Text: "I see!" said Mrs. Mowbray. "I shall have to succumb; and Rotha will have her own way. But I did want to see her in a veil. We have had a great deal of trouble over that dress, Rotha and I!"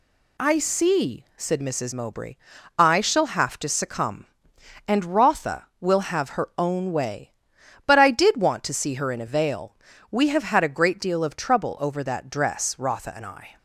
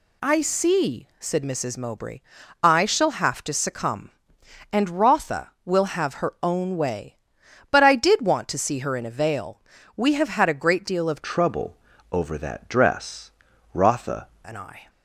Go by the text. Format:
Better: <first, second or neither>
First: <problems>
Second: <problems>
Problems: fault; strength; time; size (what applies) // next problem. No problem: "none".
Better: first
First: none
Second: changes voice from "trouble" to "Rotha"; from 11.2 to 14.2 s; 3.0 s long // pauses between "trouble" and "over"; slight; at 11.7 s; 0.34 s long